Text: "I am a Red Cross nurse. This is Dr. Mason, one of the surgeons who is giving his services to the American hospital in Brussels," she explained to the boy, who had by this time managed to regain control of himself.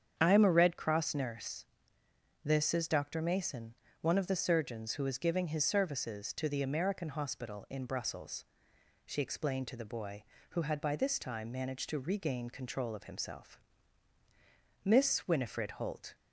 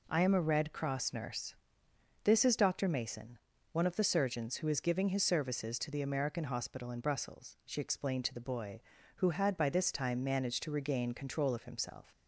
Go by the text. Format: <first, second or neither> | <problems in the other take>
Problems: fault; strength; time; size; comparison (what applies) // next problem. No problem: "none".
second | starts louder than the rest; strong; until 1.1 s; 8 dB // goes on to say "Miss Winifred Holt"; from 14.8 s on; 1.3 s long